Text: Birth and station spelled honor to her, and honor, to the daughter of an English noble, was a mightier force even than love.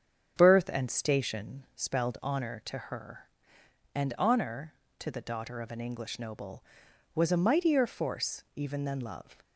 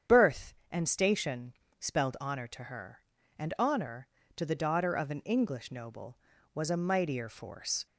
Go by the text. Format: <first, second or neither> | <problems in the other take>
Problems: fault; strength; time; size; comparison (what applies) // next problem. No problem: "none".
first | starts louder than the rest; strong; until 1.2 s; 8.5 dB; strong in the first // pauses between "station" and "spelled"; slight; at 1.5 s; 0.26 s long // stops before "even than love"; at 7.8 s